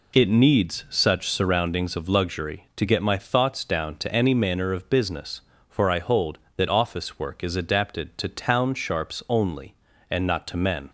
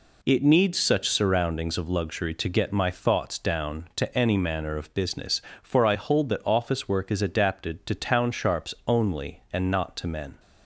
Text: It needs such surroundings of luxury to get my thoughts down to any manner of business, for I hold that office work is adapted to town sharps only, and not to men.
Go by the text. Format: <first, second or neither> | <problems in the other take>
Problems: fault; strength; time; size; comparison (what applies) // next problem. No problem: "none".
neither | none